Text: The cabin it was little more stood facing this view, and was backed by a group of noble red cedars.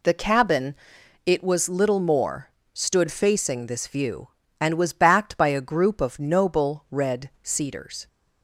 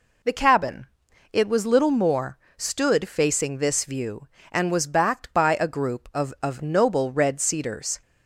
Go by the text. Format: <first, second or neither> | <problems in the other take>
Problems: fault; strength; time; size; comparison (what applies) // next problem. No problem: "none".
first | pauses between "cabin" and "it"; noticeable; at 0.8 s; 0.46 s long; noticeable in the first // pauses between "more" and "stood"; slight; at 2.3 s; 0.22 s long; slight in the first // says "of" twice; at 6.4 s